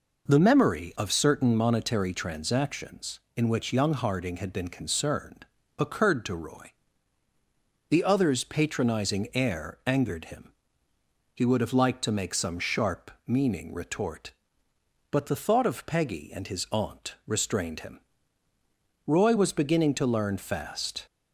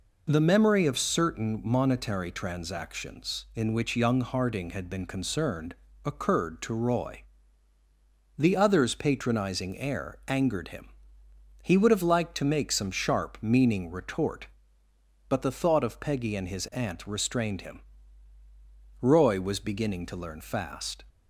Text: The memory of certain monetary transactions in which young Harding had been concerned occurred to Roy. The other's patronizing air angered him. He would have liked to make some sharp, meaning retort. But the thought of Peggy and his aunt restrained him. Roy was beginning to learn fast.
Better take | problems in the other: neither | pauses between "concerned" and "occurred"; slight; the same in both

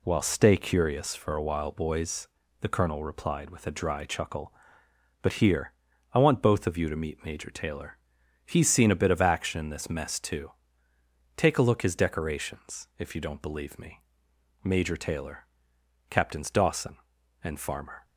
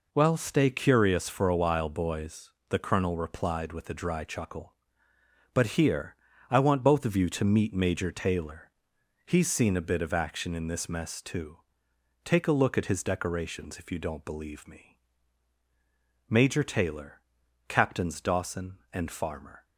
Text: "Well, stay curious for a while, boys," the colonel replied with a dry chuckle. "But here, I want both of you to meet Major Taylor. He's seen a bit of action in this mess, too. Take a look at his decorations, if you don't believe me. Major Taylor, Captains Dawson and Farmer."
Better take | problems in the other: second | skips "at"; at 11.8 s

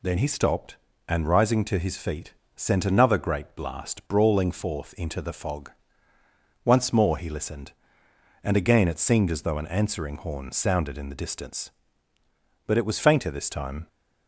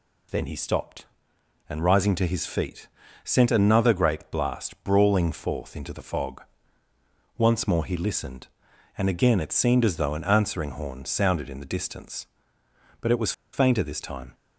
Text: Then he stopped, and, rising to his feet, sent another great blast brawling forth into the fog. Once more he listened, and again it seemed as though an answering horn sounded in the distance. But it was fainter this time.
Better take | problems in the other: first | pauses between "was" and "fainter"; slight; at 13.3 s; 0.21 s long

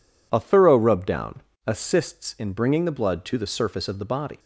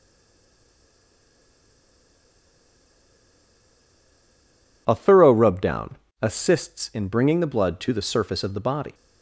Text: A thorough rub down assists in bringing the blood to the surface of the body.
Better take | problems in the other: first | stays silent before the first word; strong; until 4.8 s; 4.8 s long // pauses between "down" and "assists"; slight; at 5.9 s; 0.26 s long; slight in the first

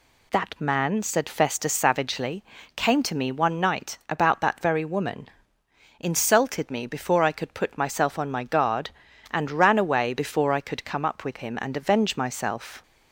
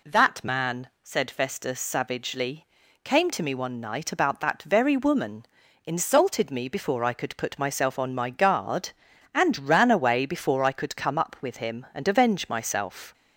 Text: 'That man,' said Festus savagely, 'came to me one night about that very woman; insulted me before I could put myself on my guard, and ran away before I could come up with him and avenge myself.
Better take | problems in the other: neither | none

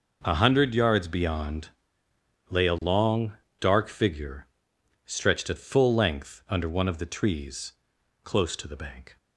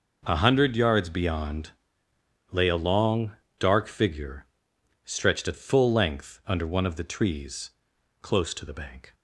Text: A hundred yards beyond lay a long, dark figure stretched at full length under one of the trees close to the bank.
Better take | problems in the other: neither | pauses between "beyond" and "lay"; noticeable; the same in both // pauses between "figure" and "stretched"; noticeable; the same in both // pauses between "trees" and "close"; noticeable; the same in both

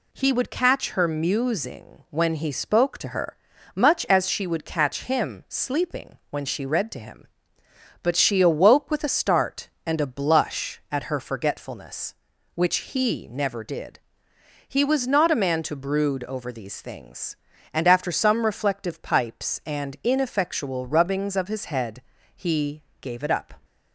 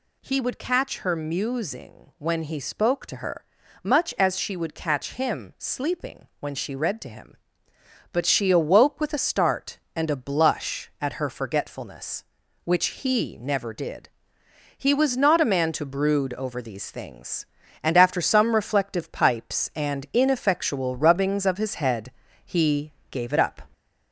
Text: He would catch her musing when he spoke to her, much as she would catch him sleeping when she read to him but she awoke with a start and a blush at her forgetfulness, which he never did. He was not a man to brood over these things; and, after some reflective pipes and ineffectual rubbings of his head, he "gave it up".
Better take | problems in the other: first | gets louder; slight; throughout; 3 dB // pauses between "he" and "gave"; slight; at 22.9 s; 0.20 s long; slight in the first

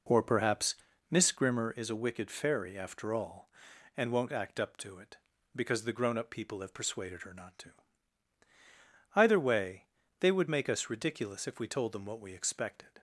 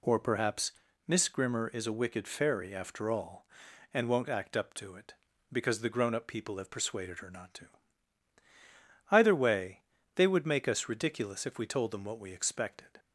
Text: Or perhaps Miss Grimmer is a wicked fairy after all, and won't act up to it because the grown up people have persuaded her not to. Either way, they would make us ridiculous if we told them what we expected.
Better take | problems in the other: second | starts louder than the rest; until 1.7 s; 4 dB // pauses between "perhaps" and "Miss"; slight; at 0.7 s; 0.36 s long; slight in the second

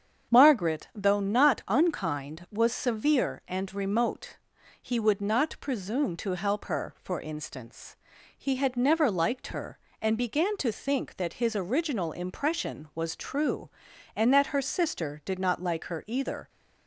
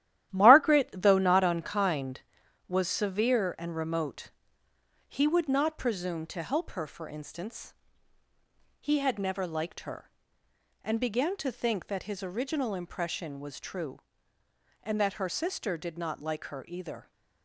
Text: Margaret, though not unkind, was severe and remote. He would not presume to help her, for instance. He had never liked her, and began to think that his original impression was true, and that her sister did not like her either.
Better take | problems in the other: first | gets quieter; strong; throughout; 8 dB // starts louder than the rest; strong; until 1.3 s; 12.5 dB; strong in the first

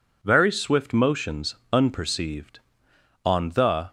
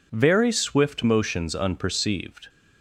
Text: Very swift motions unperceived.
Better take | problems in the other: second | pauses between "motions" and "unperceived"; slight; at 1.5 s; 0.18 s long // goes on to say "On the"; noticeable; from 3.2 s on; 0.64 s long

